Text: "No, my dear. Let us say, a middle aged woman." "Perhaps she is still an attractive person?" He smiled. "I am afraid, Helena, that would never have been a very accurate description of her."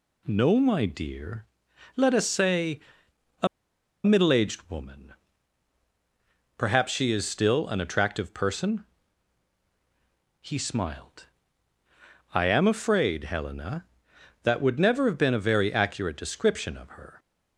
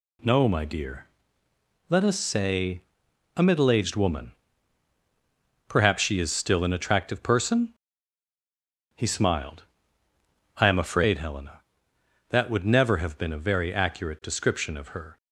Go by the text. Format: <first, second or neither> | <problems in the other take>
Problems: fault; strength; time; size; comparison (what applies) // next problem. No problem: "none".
second | pauses between "a" and "middle"; noticeable; at 3.4 s; 0.58 s long